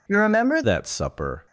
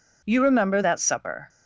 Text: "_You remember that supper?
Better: second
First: changes voice at "that"; from 0.6 s on; 0.8 s long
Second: none

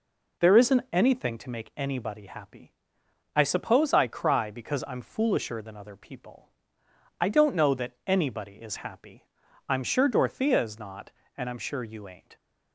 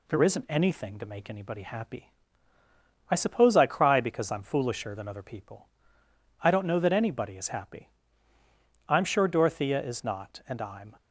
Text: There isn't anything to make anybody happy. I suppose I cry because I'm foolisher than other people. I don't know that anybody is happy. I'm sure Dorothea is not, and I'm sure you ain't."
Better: first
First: none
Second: stops before "sure you ain't"; at 10.9 s

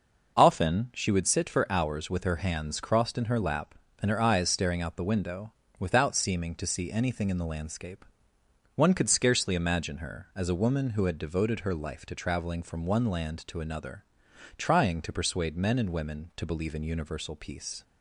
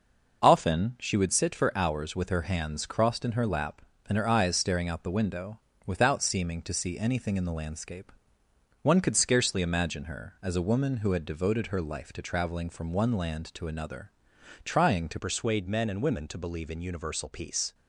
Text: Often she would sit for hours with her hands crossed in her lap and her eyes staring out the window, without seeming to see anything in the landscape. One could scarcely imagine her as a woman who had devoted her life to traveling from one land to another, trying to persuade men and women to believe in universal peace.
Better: first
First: none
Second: changes voice at "persuade"; from 15.1 s on; 2.6 s long

